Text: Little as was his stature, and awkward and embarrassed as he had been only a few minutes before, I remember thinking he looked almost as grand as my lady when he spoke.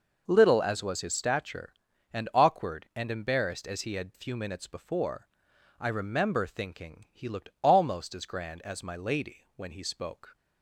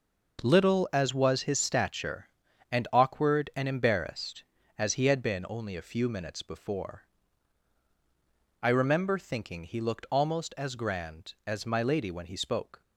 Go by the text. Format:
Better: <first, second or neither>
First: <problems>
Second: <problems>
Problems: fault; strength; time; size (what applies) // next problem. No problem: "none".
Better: second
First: skips "been only a"; at 4.1 s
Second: none